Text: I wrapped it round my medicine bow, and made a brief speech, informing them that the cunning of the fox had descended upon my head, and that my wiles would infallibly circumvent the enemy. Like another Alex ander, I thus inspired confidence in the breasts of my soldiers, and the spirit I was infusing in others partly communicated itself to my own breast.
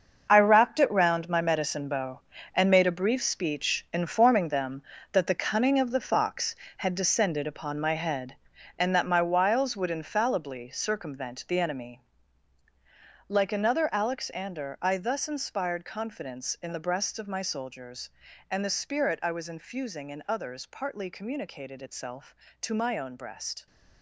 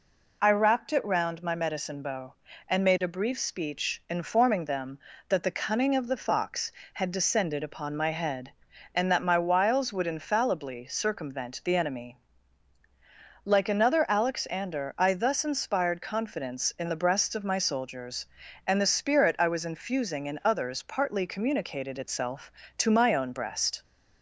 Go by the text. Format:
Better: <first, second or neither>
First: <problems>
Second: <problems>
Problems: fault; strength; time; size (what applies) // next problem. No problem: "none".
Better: second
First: gets quieter; strong; throughout; 11.5 dB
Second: none